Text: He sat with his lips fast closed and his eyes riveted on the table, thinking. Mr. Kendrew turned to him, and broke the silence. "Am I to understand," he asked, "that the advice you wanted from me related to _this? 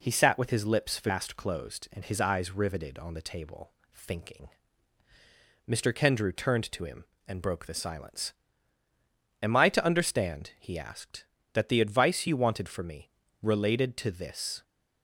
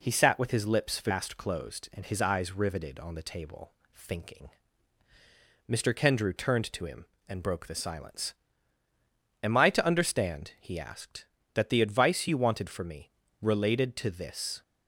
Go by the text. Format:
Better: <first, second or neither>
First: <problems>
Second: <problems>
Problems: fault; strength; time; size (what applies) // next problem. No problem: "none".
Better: neither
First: pauses between "me" and "related"; slight; at 13.1 s; 0.32 s long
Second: pauses between "me" and "related"; slight; at 13.1 s; 0.30 s long